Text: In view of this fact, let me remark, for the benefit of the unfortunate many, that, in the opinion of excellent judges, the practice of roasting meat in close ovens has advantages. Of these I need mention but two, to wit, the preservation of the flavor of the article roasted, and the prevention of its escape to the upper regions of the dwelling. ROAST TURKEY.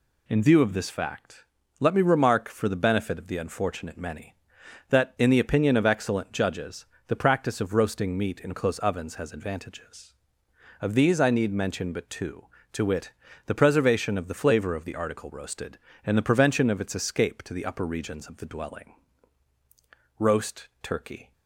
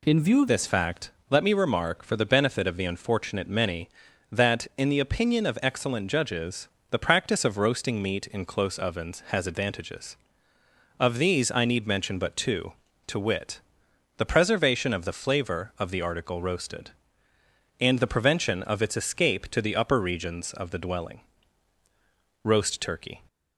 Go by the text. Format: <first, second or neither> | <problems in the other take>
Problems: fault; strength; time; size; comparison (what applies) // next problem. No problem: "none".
first | changes voice at "this"; from 0.4 s on; 22.8 s long